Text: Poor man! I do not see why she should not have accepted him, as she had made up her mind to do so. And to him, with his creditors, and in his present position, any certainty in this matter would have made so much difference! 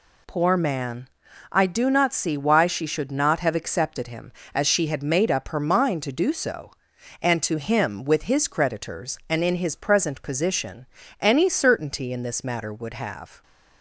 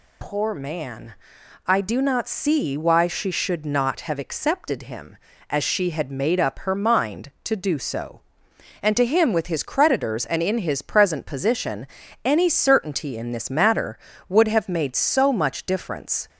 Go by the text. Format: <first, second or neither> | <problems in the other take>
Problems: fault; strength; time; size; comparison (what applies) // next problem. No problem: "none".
second | stops before "made so much difference"; at 13.4 s